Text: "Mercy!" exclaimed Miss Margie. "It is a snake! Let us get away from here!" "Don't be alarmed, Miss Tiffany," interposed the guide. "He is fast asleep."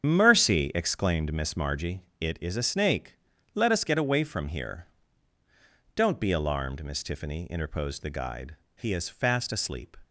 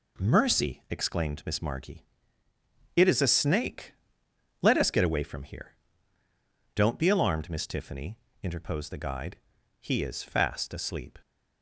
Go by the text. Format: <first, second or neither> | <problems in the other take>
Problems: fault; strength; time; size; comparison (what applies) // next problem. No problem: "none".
second | loses the start of "Mercy"; at 0.0 s; 75 ms // starts louder than the rest; strong; until 1.0 s; 8.5 dB